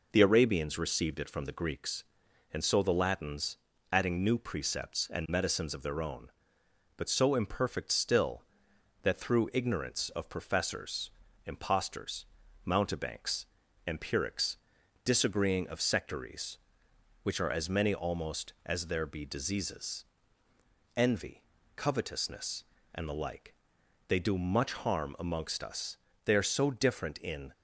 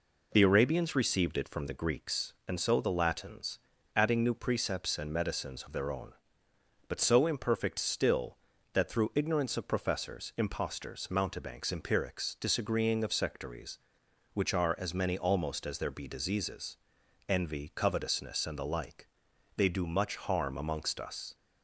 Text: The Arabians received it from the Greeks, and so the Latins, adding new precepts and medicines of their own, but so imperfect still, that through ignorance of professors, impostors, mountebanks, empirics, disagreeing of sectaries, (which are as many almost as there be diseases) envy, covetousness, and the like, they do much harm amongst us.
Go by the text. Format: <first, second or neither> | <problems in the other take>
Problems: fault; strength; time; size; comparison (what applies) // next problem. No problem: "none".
second | goes on to say "They are so different in"; noticeable; from 26.2 s on; 1.2 s long